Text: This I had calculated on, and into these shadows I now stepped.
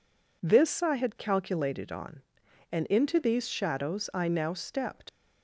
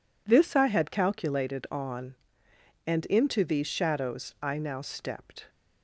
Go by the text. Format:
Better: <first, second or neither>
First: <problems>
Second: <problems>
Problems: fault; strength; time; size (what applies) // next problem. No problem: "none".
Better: second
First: leaves "stepped" unfinished; at 5.0 s; 80 ms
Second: none